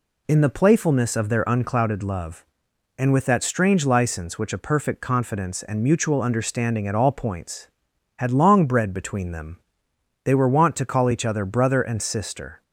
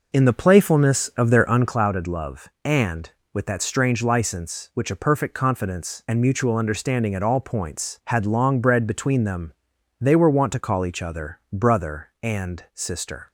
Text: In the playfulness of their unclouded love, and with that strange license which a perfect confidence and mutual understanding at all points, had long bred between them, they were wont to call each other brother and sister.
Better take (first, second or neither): first